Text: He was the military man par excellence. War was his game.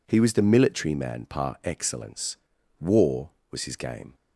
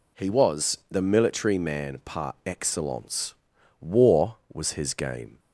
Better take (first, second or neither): neither